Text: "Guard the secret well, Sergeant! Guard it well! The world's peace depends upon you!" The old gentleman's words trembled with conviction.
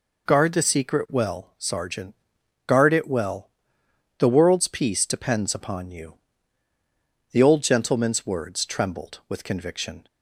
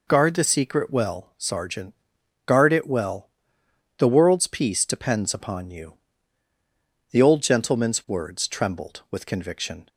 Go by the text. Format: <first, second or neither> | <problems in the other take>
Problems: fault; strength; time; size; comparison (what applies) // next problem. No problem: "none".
neither | none